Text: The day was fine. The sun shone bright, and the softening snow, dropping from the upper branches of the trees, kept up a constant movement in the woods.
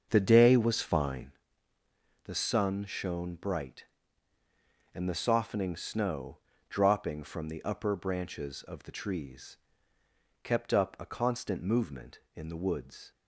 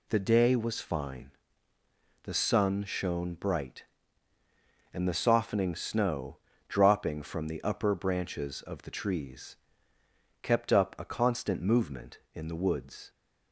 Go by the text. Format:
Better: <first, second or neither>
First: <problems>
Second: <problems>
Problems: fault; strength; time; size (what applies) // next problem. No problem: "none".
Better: second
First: starts louder than the rest; until 1.4 s; 6.5 dB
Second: none